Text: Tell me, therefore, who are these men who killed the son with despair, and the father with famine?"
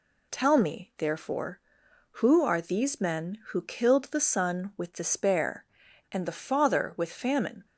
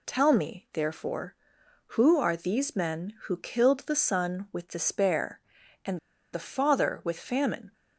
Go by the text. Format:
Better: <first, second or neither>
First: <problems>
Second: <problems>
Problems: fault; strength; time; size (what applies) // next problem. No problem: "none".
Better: first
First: none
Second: pauses between "and" and "the"; slight; at 5.9 s; 0.34 s long